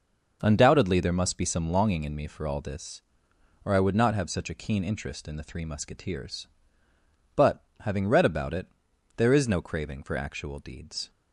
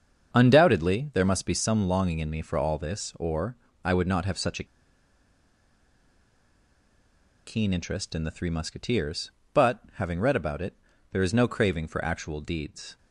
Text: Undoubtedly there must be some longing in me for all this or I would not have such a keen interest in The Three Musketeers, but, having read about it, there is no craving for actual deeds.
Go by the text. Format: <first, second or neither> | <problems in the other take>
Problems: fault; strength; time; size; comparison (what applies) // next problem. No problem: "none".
first | starts louder than the rest; until 1.3 s; 7 dB // pauses between "or" and "I"; slight; at 3.5 s; 0.28 s long // pauses between "a" and "keen"; strong; at 4.6 s; 2.8 s long